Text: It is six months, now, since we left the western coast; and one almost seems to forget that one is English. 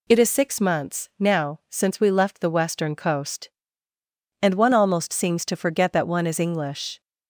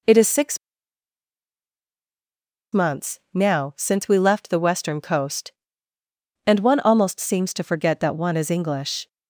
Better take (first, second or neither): first